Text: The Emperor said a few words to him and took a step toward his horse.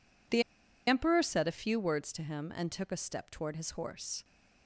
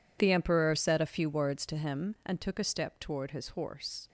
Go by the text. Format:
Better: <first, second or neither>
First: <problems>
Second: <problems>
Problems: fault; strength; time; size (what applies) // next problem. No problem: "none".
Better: second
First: pauses between "The" and "Emperor"; at 0.4 s; 0.45 s long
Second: none